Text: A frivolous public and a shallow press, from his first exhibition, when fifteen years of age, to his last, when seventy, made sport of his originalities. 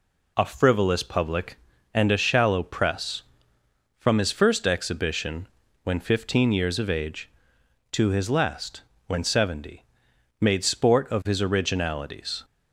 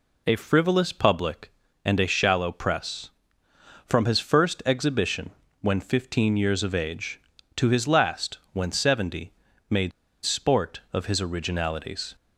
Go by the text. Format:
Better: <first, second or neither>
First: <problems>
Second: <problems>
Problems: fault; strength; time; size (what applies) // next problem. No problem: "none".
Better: first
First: none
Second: pauses between "made" and "sport"; slight; at 9.9 s; 0.31 s long